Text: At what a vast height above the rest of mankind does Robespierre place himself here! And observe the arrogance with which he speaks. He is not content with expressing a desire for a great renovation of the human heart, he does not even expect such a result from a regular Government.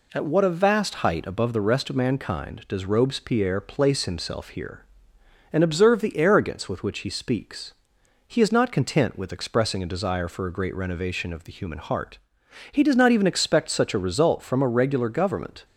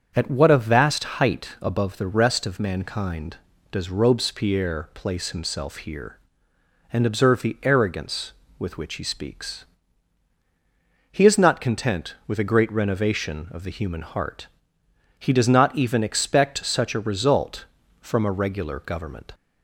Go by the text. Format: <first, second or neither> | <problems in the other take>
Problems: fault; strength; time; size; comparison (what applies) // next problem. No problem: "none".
first | starts louder than the rest; strong; until 1.1 s; 7 dB // skips "expressing a desire for"; at 12.3 s